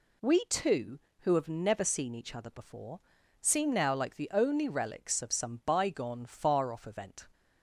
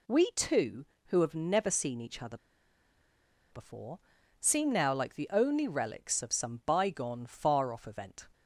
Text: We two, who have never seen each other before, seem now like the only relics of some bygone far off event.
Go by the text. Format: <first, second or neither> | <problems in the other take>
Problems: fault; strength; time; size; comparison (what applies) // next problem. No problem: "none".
first | pauses between "other" and "before"; at 2.3 s; 1.1 s long